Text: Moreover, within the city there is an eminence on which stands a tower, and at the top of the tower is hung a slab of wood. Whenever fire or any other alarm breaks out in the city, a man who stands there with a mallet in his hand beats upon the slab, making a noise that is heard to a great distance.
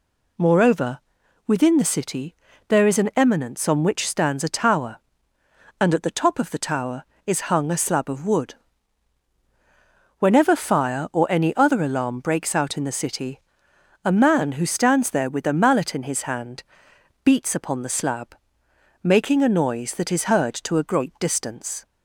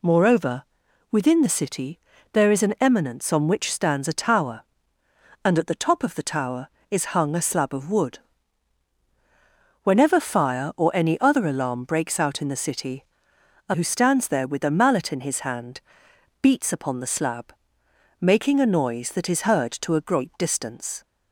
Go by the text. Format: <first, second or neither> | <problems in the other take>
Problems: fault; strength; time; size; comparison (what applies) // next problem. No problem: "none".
first | pauses between "city" and "there"; slight; at 1.9 s; 0.34 s long; slight in the first // skips "man"; at 13.7 s // pauses between "hand" and "beats"; noticeable; at 15.7 s; 0.62 s long; noticeable in the first